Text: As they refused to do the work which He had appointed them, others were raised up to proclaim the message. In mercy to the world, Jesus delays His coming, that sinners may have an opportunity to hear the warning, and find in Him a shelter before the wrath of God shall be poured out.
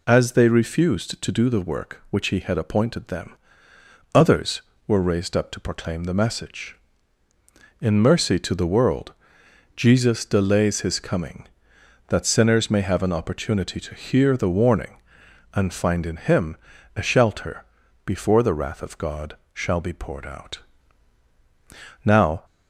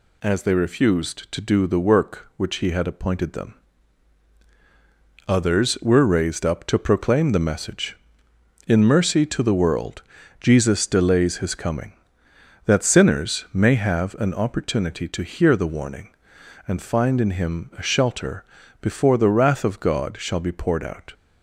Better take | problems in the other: second | pauses between "Him" and "a"; at 16.5 s; 0.40 s long // pauses between "shelter" and "before"; at 17.6 s; 0.40 s long; also in the second // pauses between "God" and "shall"; slight; at 19.3 s; 0.18 s long // goes on to say "Now"; slight; from 22.0 s on; 0.40 s long

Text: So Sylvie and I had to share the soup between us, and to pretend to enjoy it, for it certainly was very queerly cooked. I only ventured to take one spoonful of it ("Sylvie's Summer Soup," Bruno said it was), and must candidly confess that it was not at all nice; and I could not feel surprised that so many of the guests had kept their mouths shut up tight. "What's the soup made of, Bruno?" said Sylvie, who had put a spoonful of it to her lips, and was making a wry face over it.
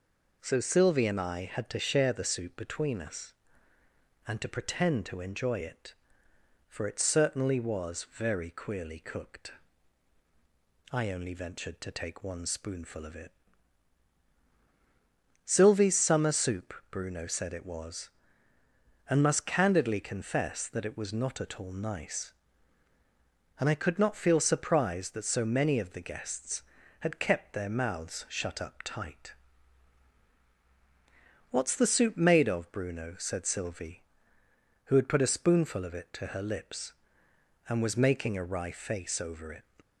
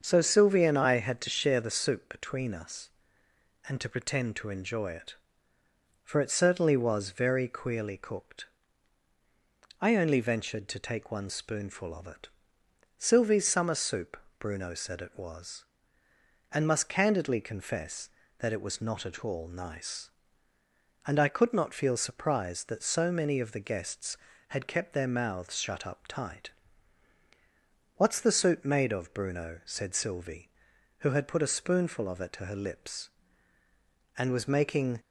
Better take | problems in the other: first | starts louder than the rest; until 1.0 s; 6.5 dB // stops before "a wry face over it"; at 34.9 s

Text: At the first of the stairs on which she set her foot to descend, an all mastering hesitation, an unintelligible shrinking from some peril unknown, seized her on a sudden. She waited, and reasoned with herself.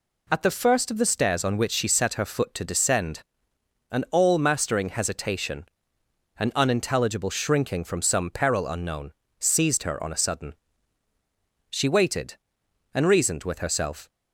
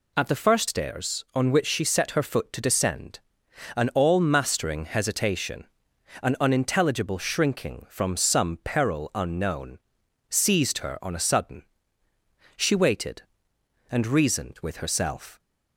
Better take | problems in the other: first | skips "of the"; at 0.6 s

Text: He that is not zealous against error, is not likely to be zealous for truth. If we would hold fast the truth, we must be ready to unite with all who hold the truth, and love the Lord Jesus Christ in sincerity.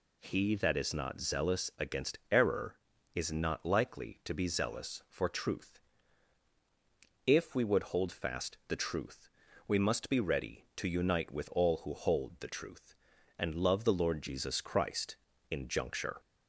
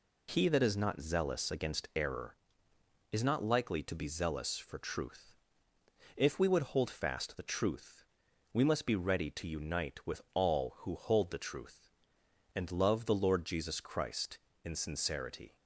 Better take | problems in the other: second | says "juncture" for "sincerity"; at 15.6 s

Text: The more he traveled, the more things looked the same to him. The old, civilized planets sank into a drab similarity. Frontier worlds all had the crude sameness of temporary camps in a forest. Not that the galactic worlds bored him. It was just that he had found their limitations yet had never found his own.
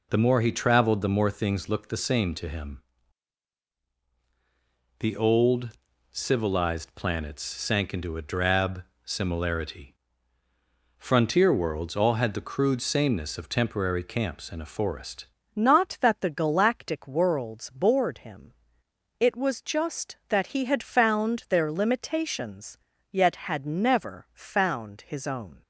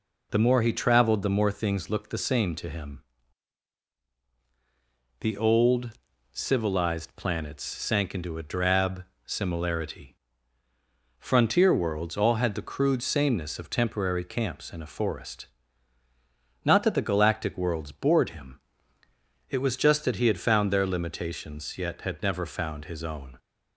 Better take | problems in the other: second | pauses between "drab" and "similarity"; slight; at 8.8 s; 0.22 s long; slight in the second // changes voice at "Not"; from 15.5 s on; 10.1 s long // pauses between "limitations" and "yet"; slight; at 22.7 s; 0.36 s long

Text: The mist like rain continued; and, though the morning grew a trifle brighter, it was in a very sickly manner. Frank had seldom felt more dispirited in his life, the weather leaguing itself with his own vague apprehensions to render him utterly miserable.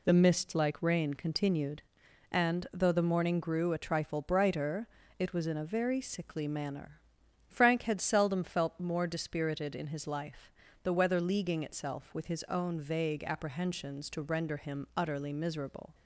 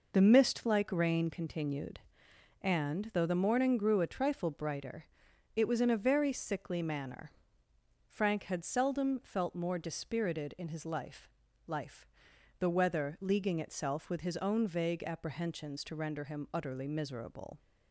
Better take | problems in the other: first | says "life" twice; at 11.6 s

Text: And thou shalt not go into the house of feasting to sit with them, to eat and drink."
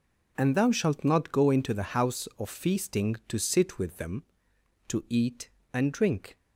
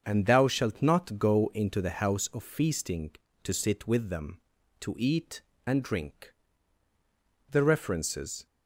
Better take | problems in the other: first | starts louder than the rest; until 1.0 s; 7 dB // goes on to say "The references"; noticeable; from 7.4 s on; 0.96 s long

